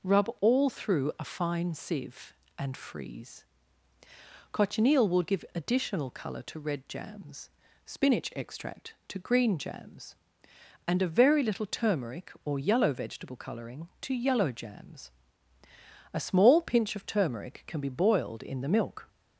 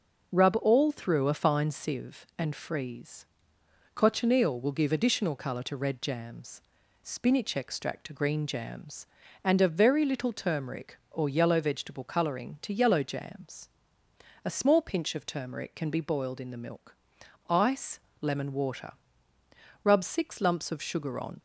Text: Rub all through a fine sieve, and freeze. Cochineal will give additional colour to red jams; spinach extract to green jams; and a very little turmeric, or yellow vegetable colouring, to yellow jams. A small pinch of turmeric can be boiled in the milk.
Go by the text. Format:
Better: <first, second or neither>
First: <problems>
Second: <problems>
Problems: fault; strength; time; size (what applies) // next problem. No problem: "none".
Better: first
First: none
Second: goes on to say "ICE LEMON WATER Rub six lumps of sugar on"; strong; from 17.4 s on; 3.9 s long